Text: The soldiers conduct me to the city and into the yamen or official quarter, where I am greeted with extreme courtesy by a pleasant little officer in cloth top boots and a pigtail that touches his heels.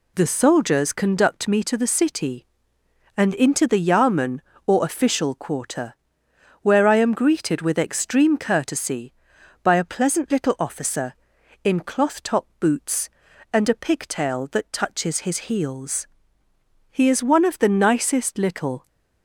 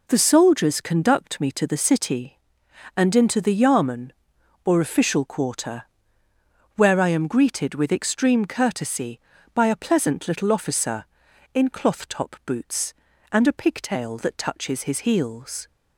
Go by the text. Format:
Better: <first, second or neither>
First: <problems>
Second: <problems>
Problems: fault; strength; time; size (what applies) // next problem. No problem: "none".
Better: second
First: goes on to say "He is one of the nicest little"; strong; from 16.9 s on; 1.9 s long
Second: none